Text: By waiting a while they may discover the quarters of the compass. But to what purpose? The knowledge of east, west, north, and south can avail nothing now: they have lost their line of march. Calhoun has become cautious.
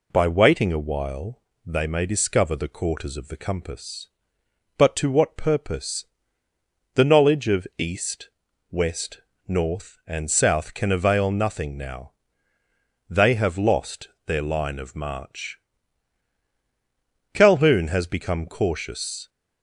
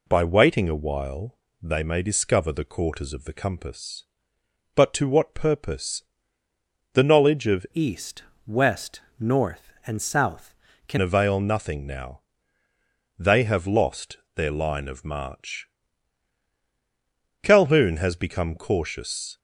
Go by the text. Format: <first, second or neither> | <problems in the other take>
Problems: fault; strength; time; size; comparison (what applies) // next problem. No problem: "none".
first | pauses between "while" and "they"; slight; at 1.3 s; 0.24 s long; slight in the first // changes voice from "east" to "can"; from 7.7 to 10.9 s; 3.2 s long // pauses between "lost" and "their"; slight; at 14.1 s; 0.16 s long; slight in the first